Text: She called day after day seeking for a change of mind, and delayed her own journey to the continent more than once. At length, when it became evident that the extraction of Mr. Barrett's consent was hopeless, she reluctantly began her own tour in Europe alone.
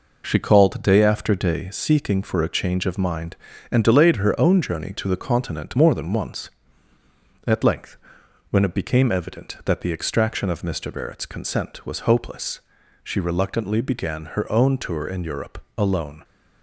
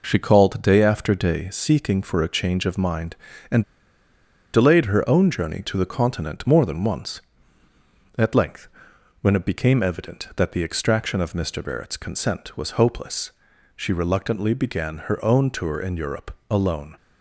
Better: first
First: pauses between "Europe" and "alone"; slight; at 15.5 s; 0.16 s long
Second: pauses between "and" and "delayed"; noticeable; at 3.6 s; 0.90 s long // pauses between "Europe" and "alone"; slight; at 16.3 s; 0.16 s long

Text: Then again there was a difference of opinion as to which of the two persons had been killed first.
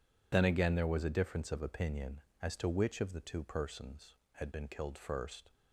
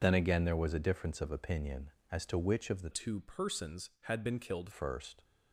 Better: first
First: none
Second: changes voice from "two" to "killed"; from 2.9 to 4.7 s; 1.8 s long

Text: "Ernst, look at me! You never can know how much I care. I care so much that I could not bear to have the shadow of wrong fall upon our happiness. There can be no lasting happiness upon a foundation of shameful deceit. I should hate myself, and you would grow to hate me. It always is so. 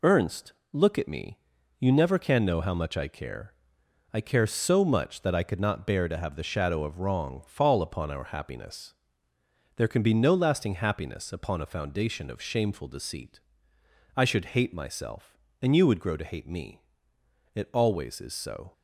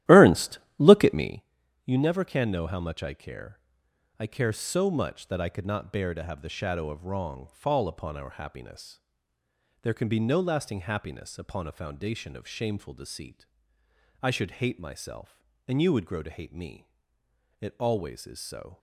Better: first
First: none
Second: starts louder than the rest; strong; until 1.5 s; 14 dB

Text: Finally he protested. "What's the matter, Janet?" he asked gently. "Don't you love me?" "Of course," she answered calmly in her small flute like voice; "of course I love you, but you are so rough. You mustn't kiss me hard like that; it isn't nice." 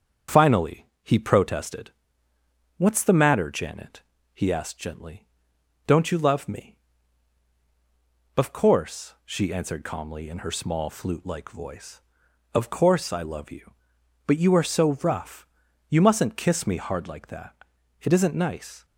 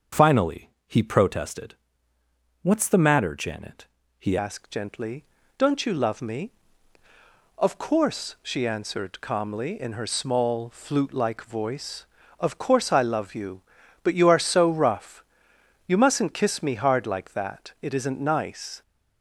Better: first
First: pauses between "Finally" and "he"; slight; at 0.8 s; 0.18 s long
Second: pauses between "Finally" and "he"; slight; at 0.6 s; 0.18 s long // changes voice at "asked"; from 4.3 s on; 14.5 s long

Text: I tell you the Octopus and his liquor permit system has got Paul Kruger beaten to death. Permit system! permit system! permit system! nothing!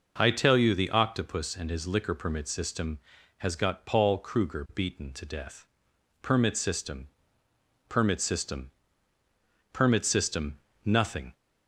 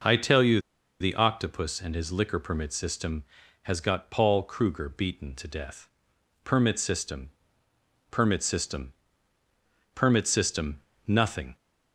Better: first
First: none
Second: pauses between "you" and "the"; at 0.5 s; 0.42 s long

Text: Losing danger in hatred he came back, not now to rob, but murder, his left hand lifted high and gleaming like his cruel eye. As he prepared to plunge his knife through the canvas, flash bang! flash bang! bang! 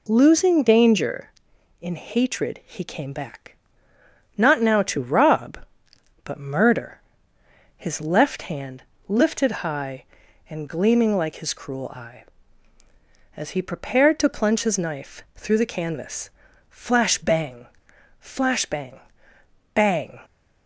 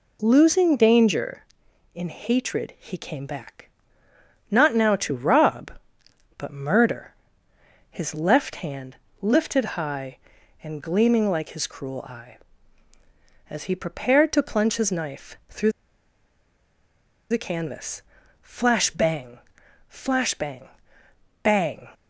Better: first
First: pauses between "hand" and "lifted"; slight; at 8.8 s; 0.26 s long // pauses between "lifted" and "high"; slight; at 9.5 s; 0.16 s long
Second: pauses between "hand" and "lifted"; slight; at 8.9 s; 0.26 s long // pauses between "lifted" and "high"; slight; at 9.6 s; 0.16 s long // pauses between "through" and "the"; strong; at 15.7 s; 1.6 s long

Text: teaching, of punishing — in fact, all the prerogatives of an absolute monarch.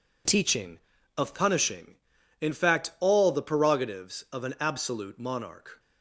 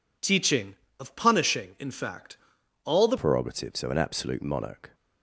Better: first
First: none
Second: changes voice at "prerogatives"; from 3.1 s on; 1.8 s long

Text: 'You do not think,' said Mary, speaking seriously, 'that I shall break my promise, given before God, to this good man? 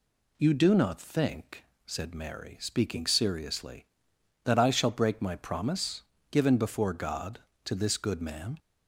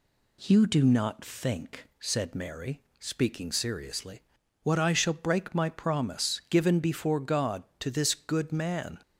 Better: first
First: none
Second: says "what" for "that"; at 4.6 s

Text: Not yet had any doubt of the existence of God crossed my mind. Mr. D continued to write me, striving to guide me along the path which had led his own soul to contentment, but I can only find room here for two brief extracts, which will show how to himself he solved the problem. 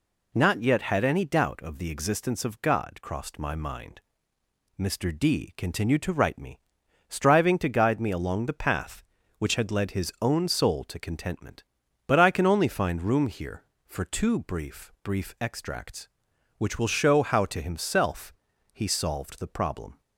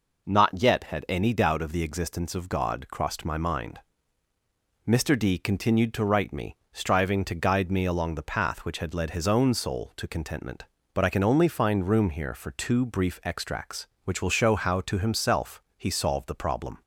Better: second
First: says "brief" twice; at 15.0 s // pauses between "himself" and "he"; at 18.3 s; 0.40 s long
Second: pauses between "himself" and "he"; slight; at 15.6 s; 0.16 s long

